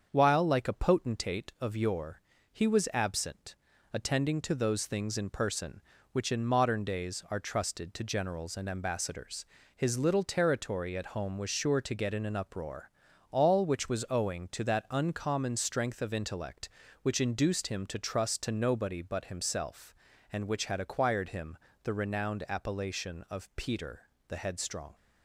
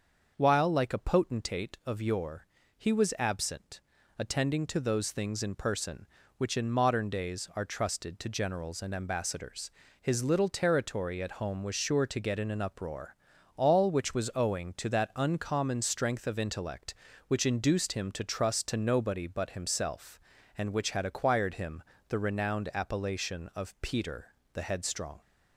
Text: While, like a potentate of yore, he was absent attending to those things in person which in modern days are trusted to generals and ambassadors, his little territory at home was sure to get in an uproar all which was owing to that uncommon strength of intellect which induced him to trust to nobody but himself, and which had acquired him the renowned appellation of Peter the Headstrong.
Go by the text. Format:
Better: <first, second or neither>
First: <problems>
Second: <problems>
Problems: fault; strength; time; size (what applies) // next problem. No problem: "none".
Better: second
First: gets quieter; slight; throughout; 2.5 dB // starts louder than the rest; until 1.1 s; 7 dB // pauses between "absent" and "attending"; at 3.5 s; 0.38 s long // pauses between "uproar" and "all"; at 12.8 s; 0.42 s long // pauses between "him" and "the"; slight; at 21.5 s; 0.28 s long // pauses between "Peter" and "the"; slight; at 24.0 s; 0.20 s long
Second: starts louder than the rest; until 1.3 s; 6.5 dB // pauses between "absent" and "attending"; at 3.8 s; 0.38 s long // pauses between "uproar" and "all"; at 13.1 s; 0.42 s long // pauses between "him" and "the"; slight; at 21.8 s; 0.28 s long // pauses between "Peter" and "the"; slight; at 24.3 s; 0.20 s long